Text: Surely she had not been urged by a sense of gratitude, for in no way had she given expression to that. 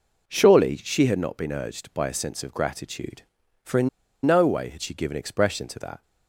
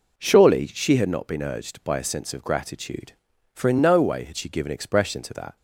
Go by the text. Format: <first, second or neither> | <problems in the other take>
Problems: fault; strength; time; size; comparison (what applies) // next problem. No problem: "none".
second | pauses between "in" and "no"; at 3.8 s; 0.36 s long